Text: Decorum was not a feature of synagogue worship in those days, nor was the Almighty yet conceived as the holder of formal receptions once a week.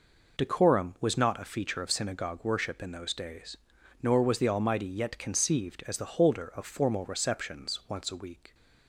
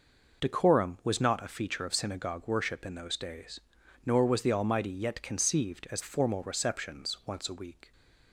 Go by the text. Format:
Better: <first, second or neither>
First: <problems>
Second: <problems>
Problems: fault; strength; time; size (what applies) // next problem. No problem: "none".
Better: first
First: none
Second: skips "the holder of"; at 6.0 s